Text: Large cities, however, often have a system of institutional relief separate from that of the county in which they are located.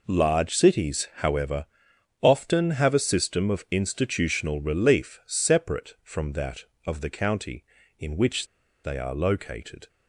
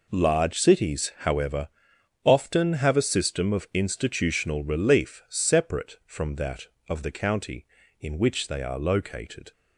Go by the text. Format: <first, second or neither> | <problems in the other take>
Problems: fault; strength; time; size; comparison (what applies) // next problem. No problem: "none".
second | pauses between "which" and "they"; at 8.4 s; 0.38 s long